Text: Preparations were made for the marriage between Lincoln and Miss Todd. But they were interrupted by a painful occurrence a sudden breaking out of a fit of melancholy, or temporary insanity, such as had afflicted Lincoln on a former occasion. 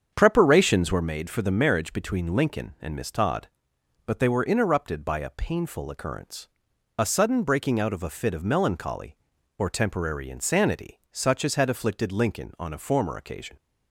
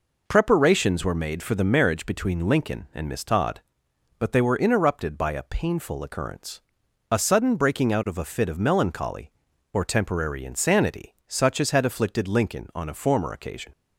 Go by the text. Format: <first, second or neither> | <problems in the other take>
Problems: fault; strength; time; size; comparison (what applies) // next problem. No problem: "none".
second | starts louder than the rest; strong; until 1.1 s; 7.5 dB // pauses between "occurrence" and "a"; noticeable; at 6.4 s; 0.50 s long; noticeable in the second